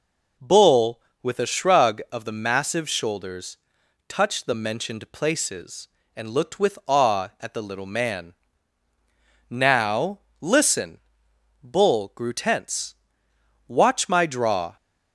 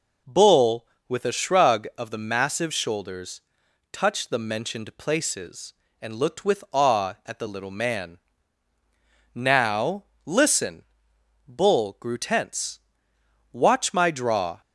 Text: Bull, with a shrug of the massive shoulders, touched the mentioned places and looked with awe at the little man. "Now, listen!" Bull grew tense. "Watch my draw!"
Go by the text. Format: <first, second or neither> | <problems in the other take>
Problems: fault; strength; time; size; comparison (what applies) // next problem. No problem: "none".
neither | none